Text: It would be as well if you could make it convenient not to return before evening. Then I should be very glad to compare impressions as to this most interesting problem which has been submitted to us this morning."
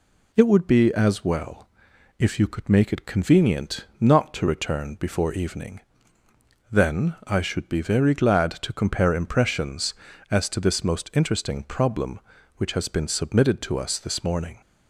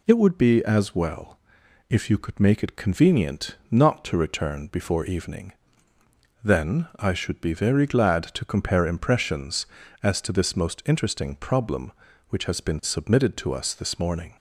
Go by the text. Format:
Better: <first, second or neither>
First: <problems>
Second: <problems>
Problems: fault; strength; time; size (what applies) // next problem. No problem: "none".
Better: neither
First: pauses between "well" and "if"; noticeable; at 1.6 s; 0.50 s long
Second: pauses between "well" and "if"; noticeable; at 1.3 s; 0.50 s long